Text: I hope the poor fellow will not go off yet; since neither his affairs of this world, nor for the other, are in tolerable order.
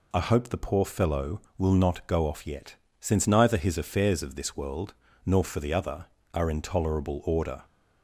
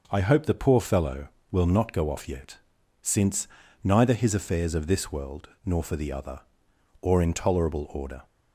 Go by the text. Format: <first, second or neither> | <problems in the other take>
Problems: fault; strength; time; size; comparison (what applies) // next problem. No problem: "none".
first | pauses between "since" and "neither"; slight; at 3.4 s; 0.34 s long // says "or" for "are"; at 7.0 s